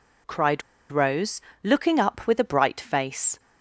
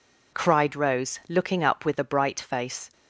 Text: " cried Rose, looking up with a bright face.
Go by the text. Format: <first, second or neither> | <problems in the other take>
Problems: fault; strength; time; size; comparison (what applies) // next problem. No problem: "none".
second | pauses between "cried" and "Rose"; slight; at 0.6 s; 0.29 s long